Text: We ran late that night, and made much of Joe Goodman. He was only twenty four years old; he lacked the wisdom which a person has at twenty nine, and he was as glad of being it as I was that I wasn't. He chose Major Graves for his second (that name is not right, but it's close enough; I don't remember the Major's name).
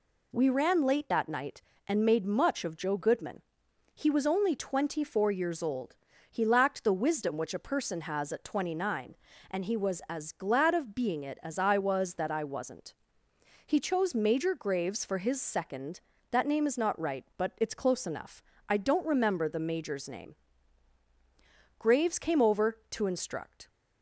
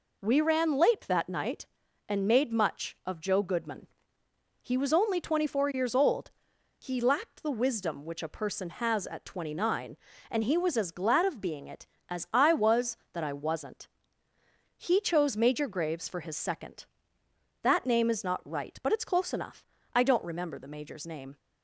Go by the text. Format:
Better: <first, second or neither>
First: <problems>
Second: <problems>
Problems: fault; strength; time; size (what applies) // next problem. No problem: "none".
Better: second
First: goes on to say "Graves came over to instruct"; strong; from 21.7 s on; 1.9 s long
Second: none